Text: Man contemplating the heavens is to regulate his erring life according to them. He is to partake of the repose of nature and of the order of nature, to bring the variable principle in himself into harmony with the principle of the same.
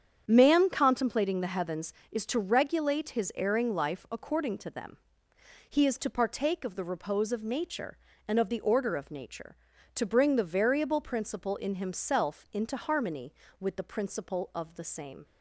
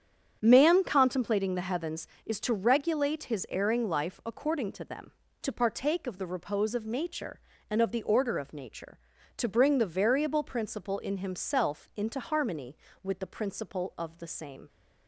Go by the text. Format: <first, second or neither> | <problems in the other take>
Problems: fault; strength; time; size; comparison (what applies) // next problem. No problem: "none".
first | starts louder than the rest; strong; until 1.4 s; 7.5 dB; strong in the first // skips "He is"; at 5.2 s